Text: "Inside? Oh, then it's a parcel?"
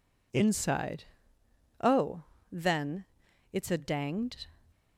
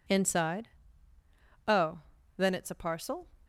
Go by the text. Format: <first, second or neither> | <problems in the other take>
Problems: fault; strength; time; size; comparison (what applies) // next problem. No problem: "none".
second | pauses between "then" and "it's"; noticeable; at 3.0 s; 0.48 s long // says "danged" for "parcel"; at 3.7 s